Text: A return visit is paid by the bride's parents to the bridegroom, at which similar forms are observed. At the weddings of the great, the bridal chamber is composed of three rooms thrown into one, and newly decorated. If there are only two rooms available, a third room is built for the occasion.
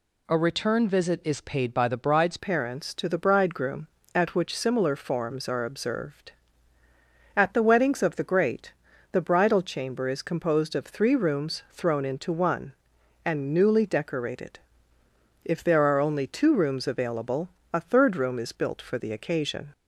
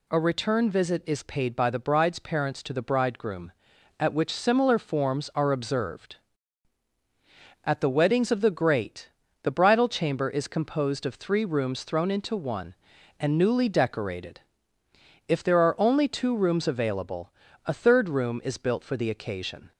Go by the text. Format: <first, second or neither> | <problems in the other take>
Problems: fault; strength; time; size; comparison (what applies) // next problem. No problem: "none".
second | changes voice at "parents"; from 2.3 s on; 17.4 s long